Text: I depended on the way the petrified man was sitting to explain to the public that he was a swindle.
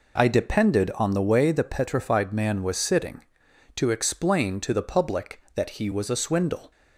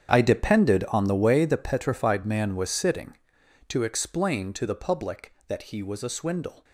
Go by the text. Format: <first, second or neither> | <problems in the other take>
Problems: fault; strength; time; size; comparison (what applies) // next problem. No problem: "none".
first | gets quieter; strong; throughout; 15.5 dB